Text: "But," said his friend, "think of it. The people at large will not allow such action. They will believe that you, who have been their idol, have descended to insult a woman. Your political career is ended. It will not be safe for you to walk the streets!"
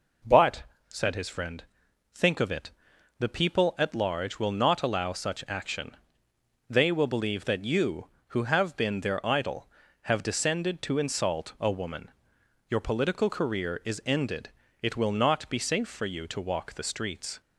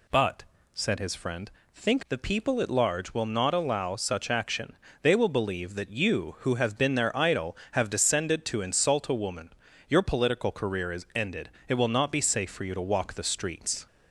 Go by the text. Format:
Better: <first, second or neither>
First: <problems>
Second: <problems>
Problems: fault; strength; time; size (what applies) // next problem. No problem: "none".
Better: first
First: none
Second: skips "of it"; at 2.0 s